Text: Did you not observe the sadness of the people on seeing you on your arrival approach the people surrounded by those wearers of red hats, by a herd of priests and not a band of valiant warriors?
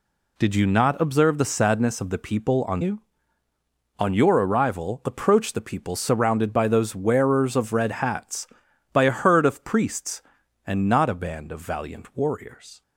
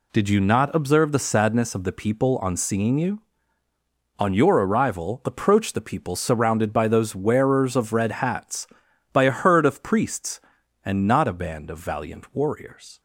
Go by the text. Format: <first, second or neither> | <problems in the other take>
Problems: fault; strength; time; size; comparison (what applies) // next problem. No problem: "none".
second | skips "seeing"; at 2.8 s